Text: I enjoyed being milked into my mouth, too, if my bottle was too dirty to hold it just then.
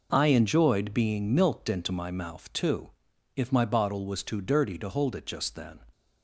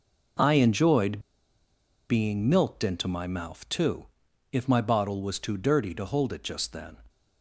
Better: first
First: none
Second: pauses between "enjoyed" and "being"; noticeable; at 1.1 s; 0.89 s long

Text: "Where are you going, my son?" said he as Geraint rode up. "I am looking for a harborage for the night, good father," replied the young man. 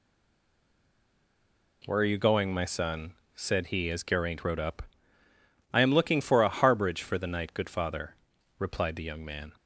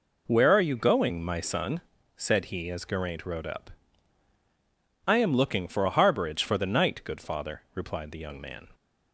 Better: second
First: stays silent before the first word; noticeable; until 1.8 s; 1.8 s long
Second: none

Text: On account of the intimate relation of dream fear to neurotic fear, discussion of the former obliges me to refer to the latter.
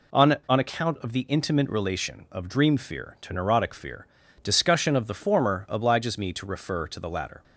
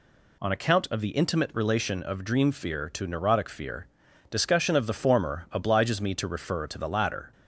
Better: second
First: says "On" twice; at 0.4 s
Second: none

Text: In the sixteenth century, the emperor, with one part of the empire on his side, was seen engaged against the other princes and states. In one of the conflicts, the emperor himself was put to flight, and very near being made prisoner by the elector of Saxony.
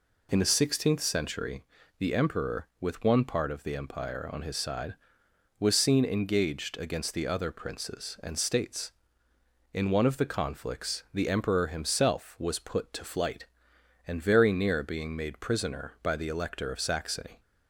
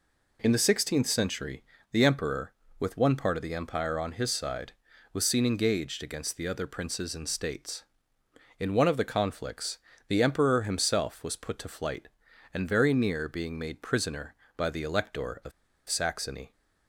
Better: first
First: none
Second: pauses between "of" and "Saxony"; at 15.5 s; 0.37 s long

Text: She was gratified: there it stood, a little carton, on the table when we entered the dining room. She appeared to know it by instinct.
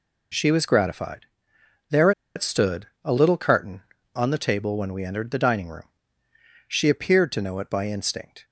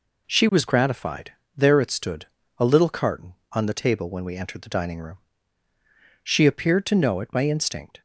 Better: second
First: pauses between "there" and "it"; slight; at 2.1 s; 0.25 s long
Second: none

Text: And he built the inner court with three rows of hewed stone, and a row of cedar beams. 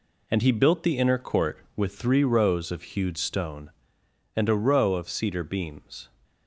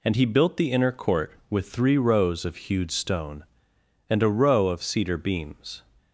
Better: second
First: gets quieter; strong; throughout; 7.5 dB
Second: none

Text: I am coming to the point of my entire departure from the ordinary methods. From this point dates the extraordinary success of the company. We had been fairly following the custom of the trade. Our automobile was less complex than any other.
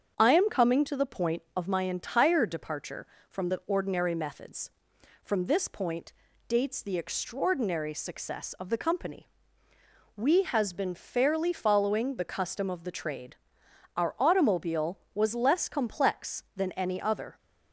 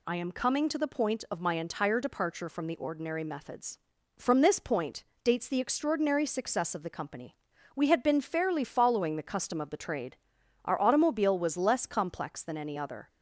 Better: second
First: starts louder than the rest; strong; until 1.1 s; 7.5 dB // pauses between "point" and "dates"; slight; at 6.1 s; 0.36 s long // says "has" for "had"; at 10.4 s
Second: pauses between "point" and "dates"; slight; at 5.0 s; 0.20 s long

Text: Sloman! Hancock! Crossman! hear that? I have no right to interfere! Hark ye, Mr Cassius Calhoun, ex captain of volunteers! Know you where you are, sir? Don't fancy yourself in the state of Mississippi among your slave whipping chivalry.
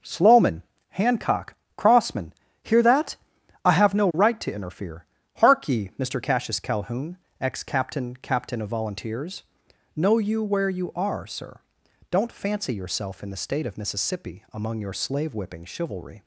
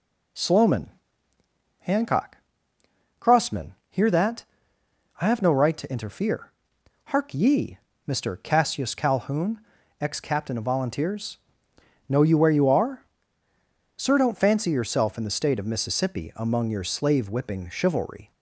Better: second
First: says "captain" twice; at 8.1 s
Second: none

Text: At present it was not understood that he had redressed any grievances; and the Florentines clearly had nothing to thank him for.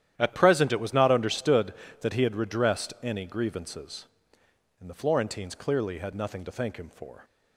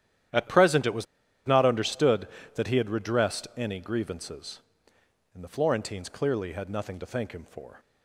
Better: first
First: starts louder than the rest; strong; until 1.1 s; 11 dB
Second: starts louder than the rest; strong; until 1.7 s; 11.5 dB // pauses between "was" and "not"; at 1.0 s; 0.42 s long

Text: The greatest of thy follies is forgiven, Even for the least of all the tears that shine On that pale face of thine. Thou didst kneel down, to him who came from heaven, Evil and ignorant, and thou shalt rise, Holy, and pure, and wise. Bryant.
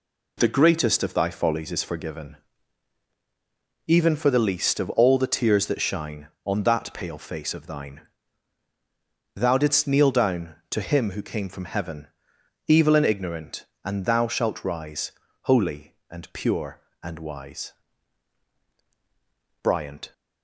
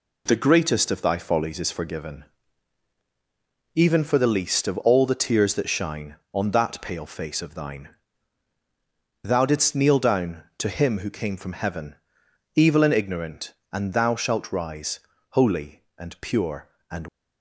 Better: first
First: none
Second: stops before "wise Bryant"; at 17.0 s

